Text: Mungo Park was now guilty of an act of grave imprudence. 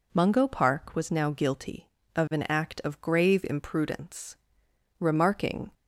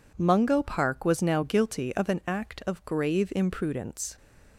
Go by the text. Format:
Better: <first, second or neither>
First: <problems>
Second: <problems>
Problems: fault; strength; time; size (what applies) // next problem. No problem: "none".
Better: second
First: goes on to say "Remarking"; noticeable; from 4.9 s on; 0.72 s long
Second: none